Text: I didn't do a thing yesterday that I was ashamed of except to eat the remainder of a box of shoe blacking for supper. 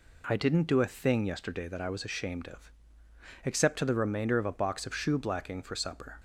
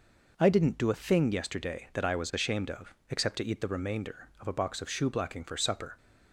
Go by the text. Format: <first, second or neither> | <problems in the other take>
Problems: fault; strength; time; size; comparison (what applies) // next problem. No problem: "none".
second | pauses between "of" and "except"; noticeable; at 2.7 s; 0.72 s long; slight in the second // skips "eat"; at 3.8 s